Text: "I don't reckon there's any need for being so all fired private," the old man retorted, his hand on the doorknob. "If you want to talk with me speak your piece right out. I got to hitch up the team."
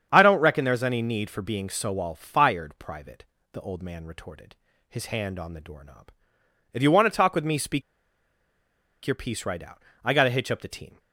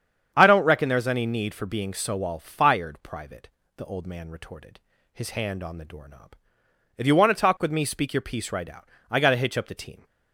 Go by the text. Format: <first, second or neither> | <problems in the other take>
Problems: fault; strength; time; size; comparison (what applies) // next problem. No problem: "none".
second | starts louder than the rest; strong; until 1.1 s; 8 dB; strong in the second // pauses between "speak" and "your"; at 7.8 s; 1.2 s long